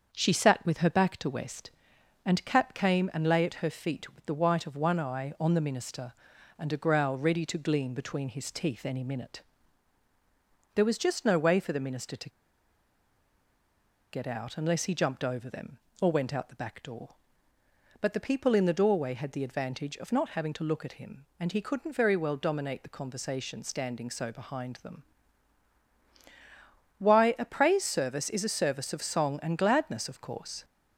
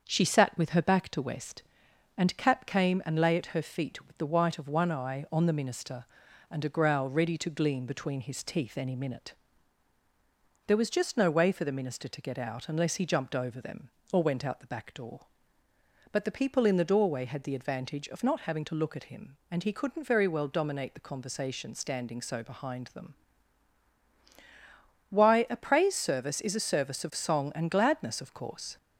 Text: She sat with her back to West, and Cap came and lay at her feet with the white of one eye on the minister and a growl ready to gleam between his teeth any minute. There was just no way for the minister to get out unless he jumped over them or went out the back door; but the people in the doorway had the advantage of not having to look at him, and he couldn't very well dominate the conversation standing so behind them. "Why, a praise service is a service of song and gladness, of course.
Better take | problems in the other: second | starts louder than the rest; until 1.1 s; 7 dB; also in the second // pauses between "to" and "get"; strong; at 12.2 s; 1.8 s long

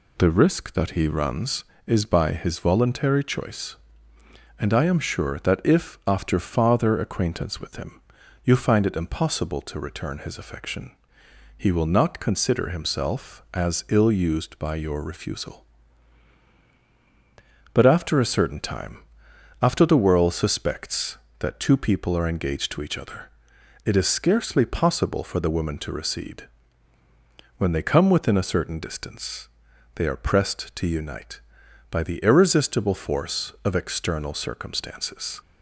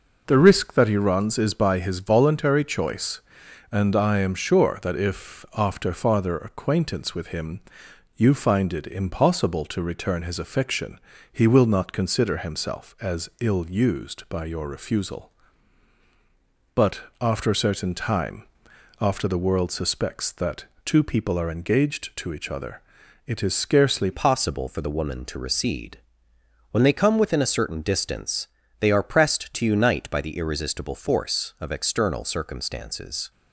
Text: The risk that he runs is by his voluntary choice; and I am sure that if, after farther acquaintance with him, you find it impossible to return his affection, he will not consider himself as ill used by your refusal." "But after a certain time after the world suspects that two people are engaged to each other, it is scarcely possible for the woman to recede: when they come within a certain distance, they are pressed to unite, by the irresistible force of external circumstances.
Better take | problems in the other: first | pauses between "But" and "after"; slight; at 17.0 s; 0.18 s long // pauses between "time" and "after"; noticeable; at 18.4 s; 0.54 s long; noticeable in the first // pauses between "that" and "two"; slight; at 20.6 s; 0.22 s long // changes voice at "possible"; from 24.1 s on; 9.2 s long

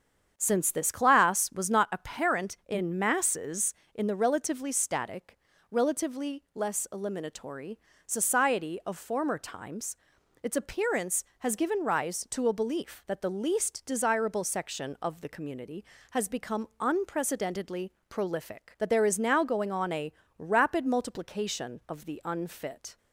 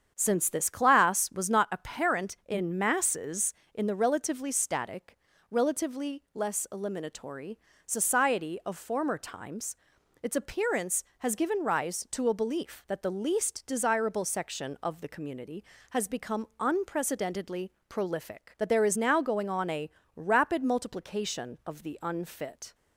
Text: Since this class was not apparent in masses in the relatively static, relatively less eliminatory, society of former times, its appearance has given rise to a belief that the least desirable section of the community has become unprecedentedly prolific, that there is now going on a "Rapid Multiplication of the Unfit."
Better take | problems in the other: neither | starts louder than the rest; strong; the same in both // pauses between "unprecedentedly" and "prolific"; slight; the same in both // pauses between "a" and "Rapid"; slight; the same in both

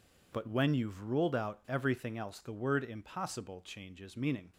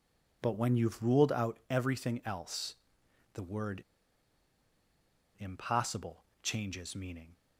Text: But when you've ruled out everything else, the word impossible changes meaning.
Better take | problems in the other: first | pauses between "word" and "impossible"; strong; at 3.8 s; 1.5 s long // pauses between "impossible" and "changes"; slight; at 6.2 s; 0.18 s long

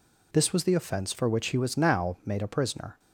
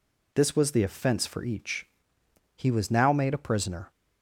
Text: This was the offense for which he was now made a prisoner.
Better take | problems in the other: first | says "each" for "which"; at 1.4 s

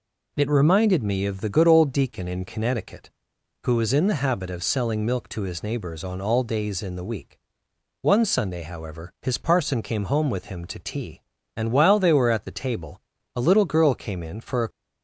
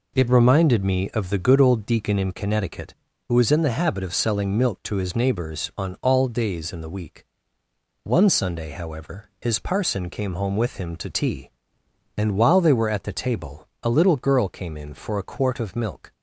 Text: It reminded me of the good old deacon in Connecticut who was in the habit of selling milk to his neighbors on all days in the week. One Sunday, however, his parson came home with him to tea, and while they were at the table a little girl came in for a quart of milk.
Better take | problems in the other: second | pauses between "table" and "a"; slight; at 12.9 s; 0.36 s long; slight in the second // stops before "quart of milk"; at 14.7 s

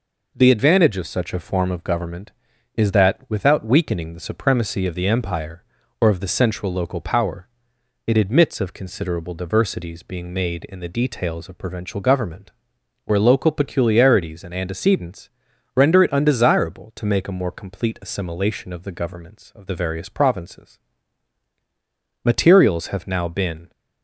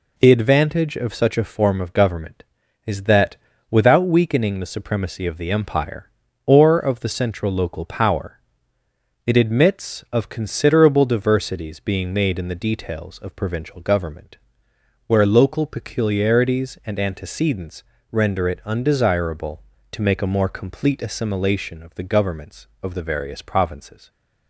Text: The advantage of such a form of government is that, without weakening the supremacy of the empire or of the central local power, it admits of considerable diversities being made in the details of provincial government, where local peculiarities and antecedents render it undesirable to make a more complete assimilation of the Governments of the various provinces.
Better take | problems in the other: second | pauses between "antecedents" and "render"; noticeable; at 15.2 s; 0.46 s long; slight in the second // goes on to say "Materials have now been"; strong; from 20.9 s on; 2.7 s long

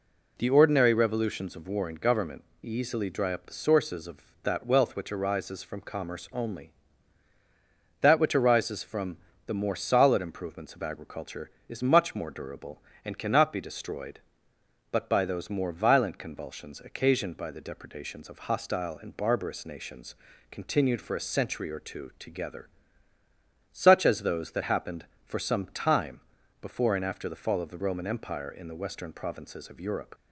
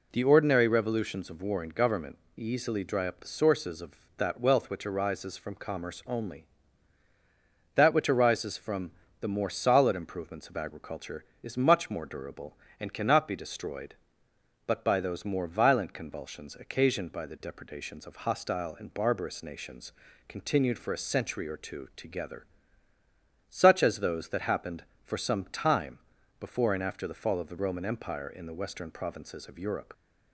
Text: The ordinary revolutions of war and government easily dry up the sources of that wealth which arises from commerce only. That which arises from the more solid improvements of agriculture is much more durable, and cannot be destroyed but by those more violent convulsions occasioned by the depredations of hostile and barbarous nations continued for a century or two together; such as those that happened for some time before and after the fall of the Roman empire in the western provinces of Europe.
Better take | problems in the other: neither | pauses between "government" and "easily"; slight; the same in both // pauses between "from" and "the"; slight; the same in both // pauses between "nations" and "continued"; the same in both // pauses between "time" and "before"; the same in both

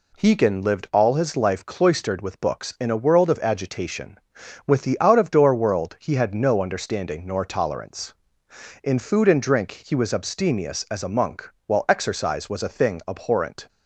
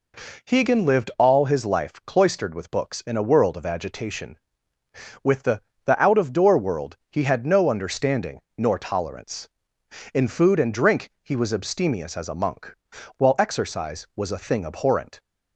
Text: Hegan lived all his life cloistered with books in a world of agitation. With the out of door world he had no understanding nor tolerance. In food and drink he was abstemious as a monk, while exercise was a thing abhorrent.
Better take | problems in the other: first | says "the" twice; at 5.8 s // pauses between "world" and "he"; slight; at 6.9 s; 0.16 s long // pauses between "understanding" and "nor"; slight; at 8.3 s; 0.18 s long

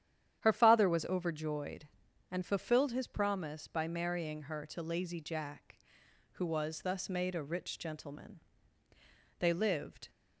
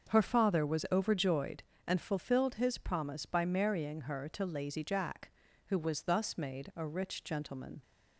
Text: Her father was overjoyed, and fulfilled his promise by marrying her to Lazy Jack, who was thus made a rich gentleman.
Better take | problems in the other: second | starts louder than the rest; strong; until 1.4 s; 10 dB; also in the second // goes on to say "They lived"; noticeable; from 9.3 s on; 0.70 s long

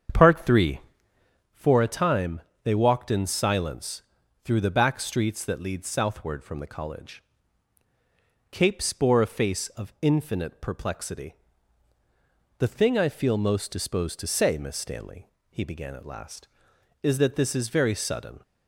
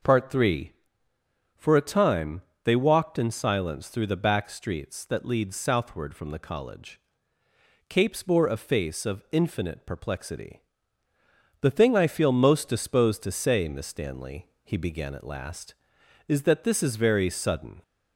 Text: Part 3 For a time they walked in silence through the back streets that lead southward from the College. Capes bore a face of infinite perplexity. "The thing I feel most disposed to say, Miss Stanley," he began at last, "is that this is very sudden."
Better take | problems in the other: second | starts louder than the rest; strong; until 1.5 s; 8 dB // pauses between "time" and "they"; slight; at 2.4 s; 0.22 s long; slight in the second // pauses between "silence" and "through"; at 4.0 s; 0.42 s long

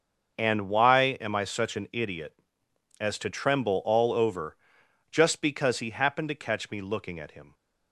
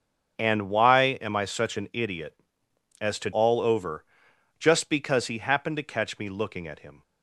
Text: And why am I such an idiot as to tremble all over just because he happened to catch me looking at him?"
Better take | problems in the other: first | starts louder than the rest; strong; until 1.4 s; 7 dB; also in the first // skips "tremble"; at 3.3 s // pauses between "over" and "just"; noticeable; at 4.0 s; 0.54 s long; noticeable in the first

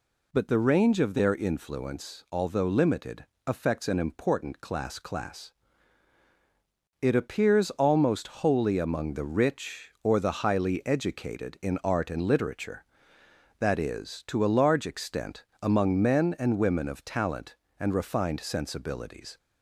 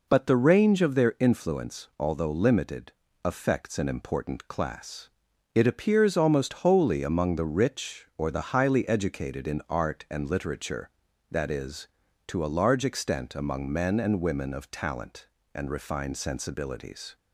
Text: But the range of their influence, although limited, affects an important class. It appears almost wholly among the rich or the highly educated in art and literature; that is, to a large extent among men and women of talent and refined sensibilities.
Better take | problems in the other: second | says "class" twice; at 4.9 s // pauses between "extent" and "among"; slight; at 15.4 s; 0.18 s long

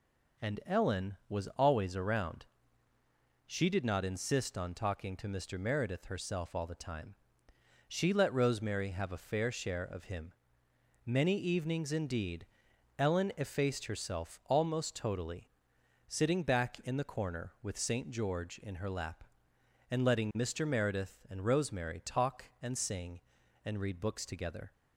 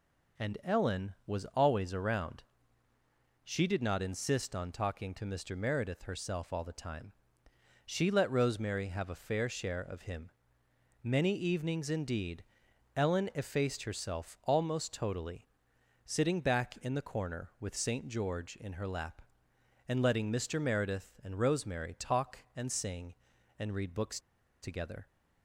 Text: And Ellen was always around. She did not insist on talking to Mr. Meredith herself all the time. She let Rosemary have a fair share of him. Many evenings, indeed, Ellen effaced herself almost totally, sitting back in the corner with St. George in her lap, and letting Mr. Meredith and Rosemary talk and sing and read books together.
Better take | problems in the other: first | pauses between "books" and "together"; at 24.1 s; 0.42 s long

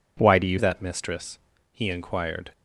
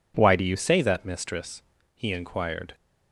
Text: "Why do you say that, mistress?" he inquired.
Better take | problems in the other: second | skips "say"; at 0.5 s

